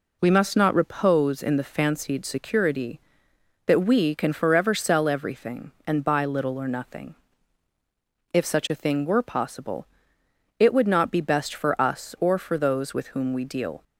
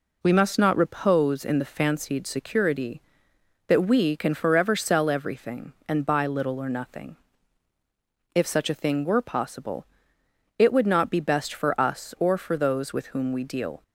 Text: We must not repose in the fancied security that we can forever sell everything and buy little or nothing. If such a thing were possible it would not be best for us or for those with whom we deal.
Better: neither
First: pauses between "possible" and "it"; noticeable; at 9.8 s; 0.72 s long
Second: pauses between "possible" and "it"; noticeable; at 9.8 s; 0.72 s long

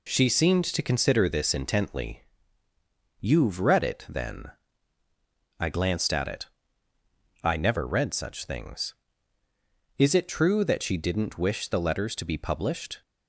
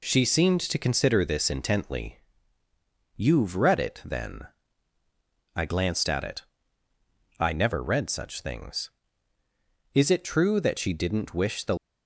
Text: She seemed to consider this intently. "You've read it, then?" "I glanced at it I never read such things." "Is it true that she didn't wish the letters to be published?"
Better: first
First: pauses between "it" and "I"; noticeable; at 6.4 s; 0.98 s long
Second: pauses between "it" and "I"; noticeable; at 6.4 s; 0.98 s long // stops before "letters to be published"; at 11.7 s

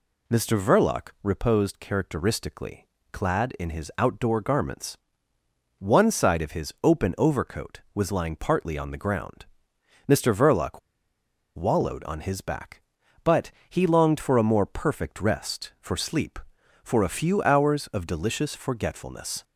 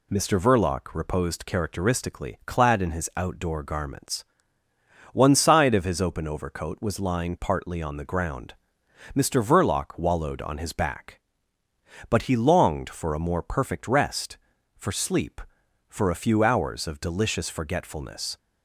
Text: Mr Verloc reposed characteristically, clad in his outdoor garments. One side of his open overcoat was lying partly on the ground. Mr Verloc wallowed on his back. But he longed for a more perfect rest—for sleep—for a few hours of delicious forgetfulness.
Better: second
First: pauses between "Verloc" and "wallowed"; noticeable; at 10.7 s; 0.77 s long // pauses between "But" and "he"; slight; at 13.5 s; 0.18 s long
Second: none

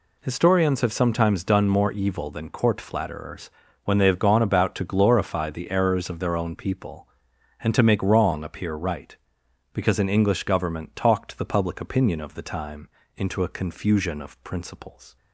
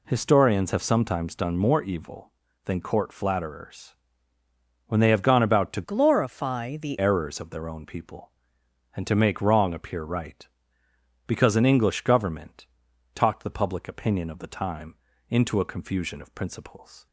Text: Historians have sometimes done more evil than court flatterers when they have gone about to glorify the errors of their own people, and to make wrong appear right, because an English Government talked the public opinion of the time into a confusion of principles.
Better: first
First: pauses between "flatterers" and "when"; slight; at 3.5 s; 0.34 s long // pauses between "time" and "into"; slight; at 12.8 s; 0.28 s long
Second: pauses between "flatterers" and "when"; noticeable; at 3.9 s; 0.90 s long // changes voice from "glorify" to "the"; from 5.8 to 6.9 s; 1.1 s long // pauses between "Government" and "talked"; noticeable; at 12.6 s; 0.48 s long // pauses between "time" and "into"; slight; at 14.9 s; 0.36 s long

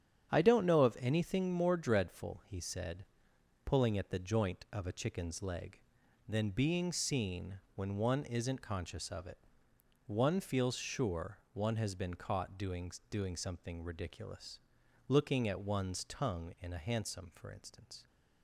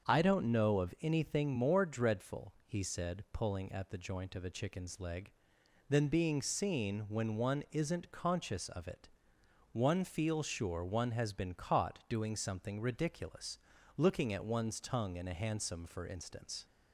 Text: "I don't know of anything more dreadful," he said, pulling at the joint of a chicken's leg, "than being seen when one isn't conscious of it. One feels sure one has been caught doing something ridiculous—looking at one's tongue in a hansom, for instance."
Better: second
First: starts louder than the rest; strong; until 1.3 s; 9 dB // says "doing" twice; at 13.0 s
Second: starts louder than the rest; until 1.1 s; 7 dB

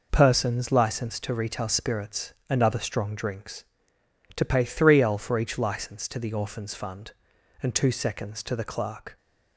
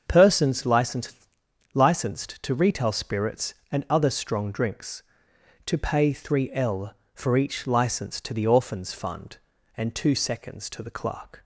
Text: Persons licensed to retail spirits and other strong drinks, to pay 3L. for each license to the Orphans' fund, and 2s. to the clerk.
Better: first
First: none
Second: starts louder than the rest; until 1.0 s; 7 dB // says "licensed" twice; at 1.7 s

